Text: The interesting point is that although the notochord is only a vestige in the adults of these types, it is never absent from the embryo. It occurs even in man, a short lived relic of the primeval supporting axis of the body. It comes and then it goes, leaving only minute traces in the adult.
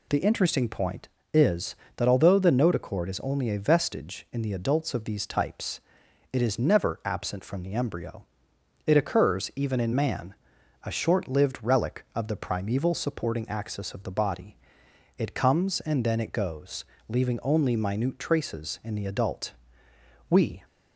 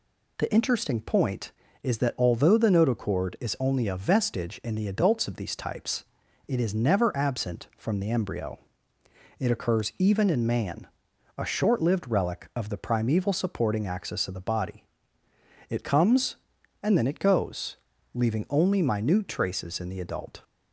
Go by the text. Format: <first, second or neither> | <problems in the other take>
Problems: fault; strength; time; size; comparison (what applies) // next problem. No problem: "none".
second | goes on to say "We"; slight; from 20.2 s on; 0.34 s long